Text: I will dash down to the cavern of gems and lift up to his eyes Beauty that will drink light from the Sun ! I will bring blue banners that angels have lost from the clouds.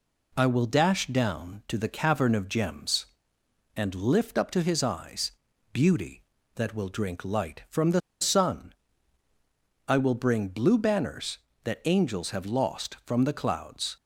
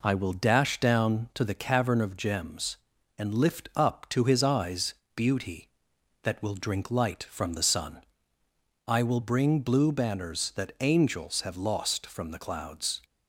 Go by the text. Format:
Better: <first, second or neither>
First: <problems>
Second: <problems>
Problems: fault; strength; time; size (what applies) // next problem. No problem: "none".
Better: second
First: pauses between "eyes" and "Beauty"; at 5.3 s; 0.40 s long // pauses between "the" and "Sun"; slight; at 8.0 s; 0.21 s long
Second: pauses between "eyes" and "Beauty"; slight; at 4.9 s; 0.20 s long